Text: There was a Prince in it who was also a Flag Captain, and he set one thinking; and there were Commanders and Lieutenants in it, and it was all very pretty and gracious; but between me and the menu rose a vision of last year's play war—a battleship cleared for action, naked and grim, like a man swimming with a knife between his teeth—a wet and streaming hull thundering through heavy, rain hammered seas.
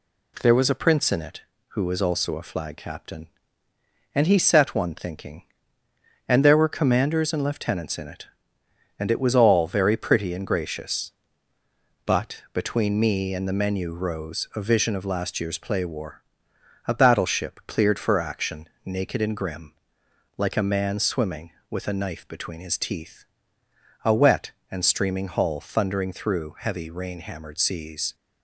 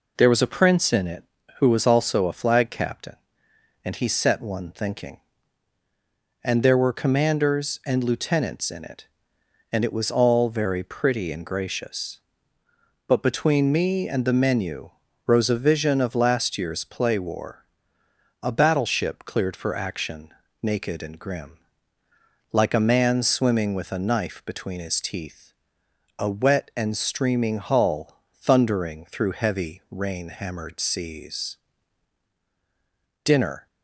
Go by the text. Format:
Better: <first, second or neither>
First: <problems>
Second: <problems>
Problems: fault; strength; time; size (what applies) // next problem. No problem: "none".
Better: first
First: none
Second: pauses between "menu" and "rose"; at 14.8 s; 0.38 s long // pauses between "hull" and "thundering"; slight; at 28.1 s; 0.18 s long // goes on to say "DINNER"; slight; from 33.2 s on; 0.42 s long